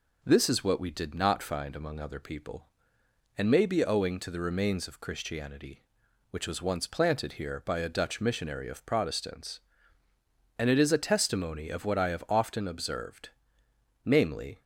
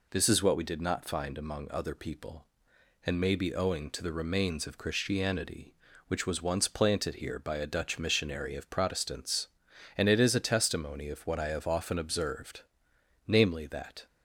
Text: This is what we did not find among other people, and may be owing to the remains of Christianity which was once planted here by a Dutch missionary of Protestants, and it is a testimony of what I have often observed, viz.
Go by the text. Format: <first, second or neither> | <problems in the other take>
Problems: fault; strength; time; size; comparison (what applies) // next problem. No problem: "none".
first | goes on to say "that"; slight; from 13.6 s on; 0.40 s long